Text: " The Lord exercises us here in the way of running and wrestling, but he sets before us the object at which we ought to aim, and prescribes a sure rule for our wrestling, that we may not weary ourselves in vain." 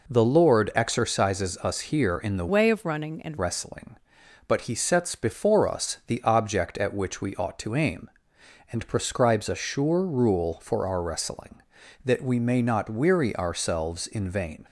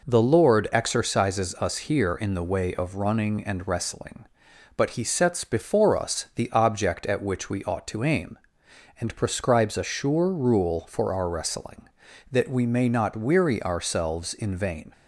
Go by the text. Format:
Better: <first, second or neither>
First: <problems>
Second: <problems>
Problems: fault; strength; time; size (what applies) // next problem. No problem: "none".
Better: second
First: changes voice from "way" to "and"; from 2.4 to 3.3 s; 0.9 s long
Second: none